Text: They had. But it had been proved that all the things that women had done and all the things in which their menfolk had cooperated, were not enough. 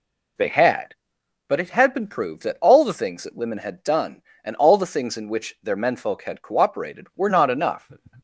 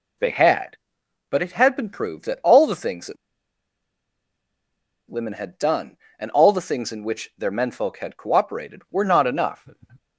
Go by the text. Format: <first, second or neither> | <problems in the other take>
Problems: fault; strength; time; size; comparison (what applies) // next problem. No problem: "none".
first | pauses between "that" and "women"; strong; at 3.1 s; 1.9 s long